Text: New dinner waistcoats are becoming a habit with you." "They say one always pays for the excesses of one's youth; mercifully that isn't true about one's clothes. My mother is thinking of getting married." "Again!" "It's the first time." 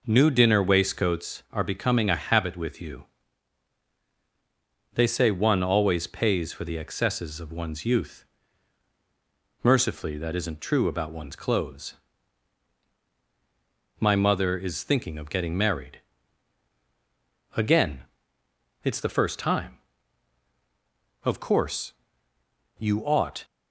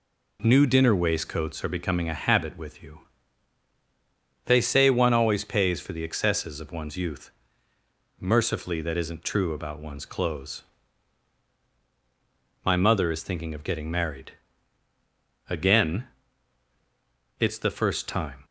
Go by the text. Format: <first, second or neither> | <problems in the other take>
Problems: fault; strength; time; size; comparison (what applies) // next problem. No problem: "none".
second | goes on to say "Of course you ought"; strong; from 21.2 s on; 2.2 s long